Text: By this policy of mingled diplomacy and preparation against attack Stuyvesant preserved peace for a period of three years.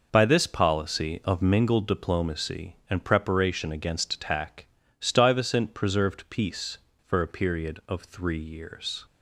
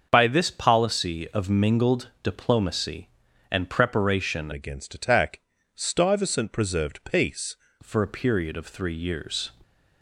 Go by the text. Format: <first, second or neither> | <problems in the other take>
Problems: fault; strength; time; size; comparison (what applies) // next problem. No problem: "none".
first | starts louder than the rest; until 1.1 s; 6.5 dB // changes voice from "against" to "peace"; from 4.5 to 7.5 s; 3.0 s long // pauses between "attack" and "Stuyvesant"; slight; at 5.3 s; 0.34 s long; slight in the first